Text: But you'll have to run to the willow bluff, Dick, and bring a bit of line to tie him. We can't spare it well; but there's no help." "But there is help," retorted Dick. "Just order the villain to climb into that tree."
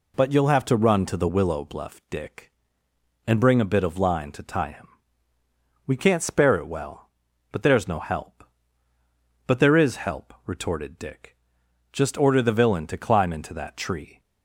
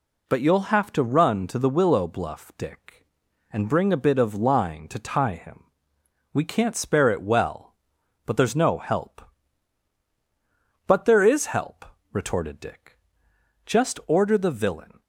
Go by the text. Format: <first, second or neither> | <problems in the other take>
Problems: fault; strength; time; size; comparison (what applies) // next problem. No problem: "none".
first | stops before "to climb into that tree"; at 15.0 s